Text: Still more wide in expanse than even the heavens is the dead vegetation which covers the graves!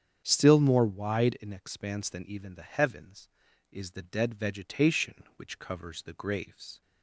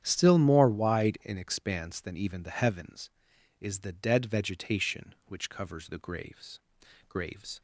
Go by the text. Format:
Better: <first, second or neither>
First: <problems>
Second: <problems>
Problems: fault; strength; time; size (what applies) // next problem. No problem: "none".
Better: first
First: starts louder than the rest; strong; until 1.2 s; 8.5 dB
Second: starts louder than the rest; strong; until 1.0 s; 9.5 dB // says "graves" twice; at 7.0 s